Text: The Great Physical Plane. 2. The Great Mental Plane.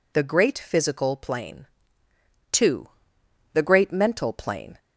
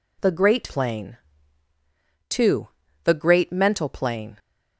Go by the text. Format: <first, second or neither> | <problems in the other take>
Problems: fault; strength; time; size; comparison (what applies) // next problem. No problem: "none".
first | skips "Physical"; at 0.6 s